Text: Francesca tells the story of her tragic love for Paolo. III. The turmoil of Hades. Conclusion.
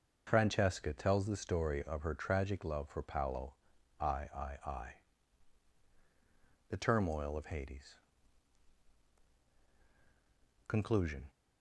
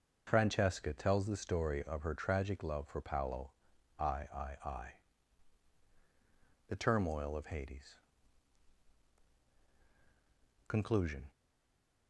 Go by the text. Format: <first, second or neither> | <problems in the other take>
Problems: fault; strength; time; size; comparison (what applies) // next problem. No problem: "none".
first | stays silent after the last word; slight; from 11.3 s on; 0.7 s long